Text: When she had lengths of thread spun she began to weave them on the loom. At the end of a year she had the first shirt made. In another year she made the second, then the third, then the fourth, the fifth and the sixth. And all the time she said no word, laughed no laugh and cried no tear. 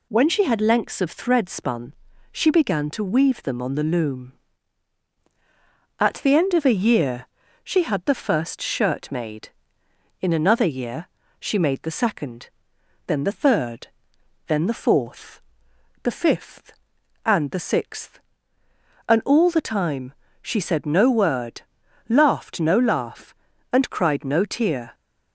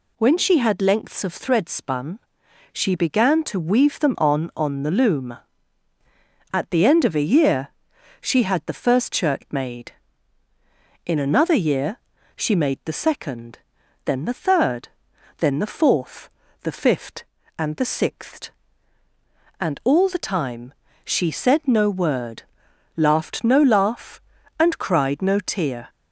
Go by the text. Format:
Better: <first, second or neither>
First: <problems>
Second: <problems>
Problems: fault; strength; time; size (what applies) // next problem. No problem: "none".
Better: first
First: pauses between "spun" and "she"; at 1.9 s; 0.40 s long // pauses between "year" and "she"; slight; at 7.2 s; 0.36 s long // pauses between "year" and "she"; slight; at 11.0 s; 0.32 s long // pauses between "time" and "she"; slight; at 20.1 s; 0.26 s long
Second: pauses between "spun" and "she"; noticeable; at 2.1 s; 0.52 s long // says "on" twice; at 4.5 s // pauses between "year" and "she"; noticeable; at 7.6 s; 0.52 s long // pauses between "year" and "she"; at 11.9 s; 0.40 s long // pauses between "time" and "she"; slight; at 20.7 s; 0.30 s long